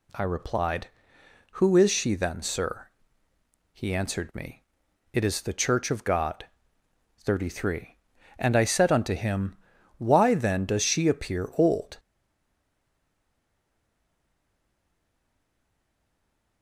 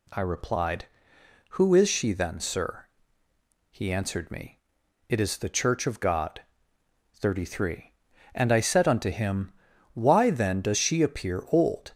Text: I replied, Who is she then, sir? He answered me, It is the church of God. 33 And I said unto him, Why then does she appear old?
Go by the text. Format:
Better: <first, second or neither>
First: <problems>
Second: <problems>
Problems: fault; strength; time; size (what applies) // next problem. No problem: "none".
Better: second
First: stays silent after the last word; strong; from 11.9 s on; 4.7 s long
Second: none